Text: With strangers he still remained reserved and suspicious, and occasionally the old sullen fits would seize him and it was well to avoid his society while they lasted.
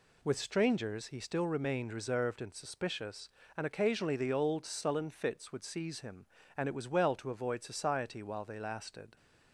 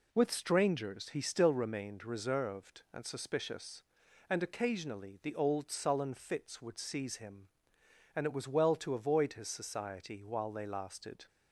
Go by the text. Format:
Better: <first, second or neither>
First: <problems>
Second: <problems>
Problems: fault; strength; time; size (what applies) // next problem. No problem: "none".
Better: second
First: skips "his"; at 7.6 s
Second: none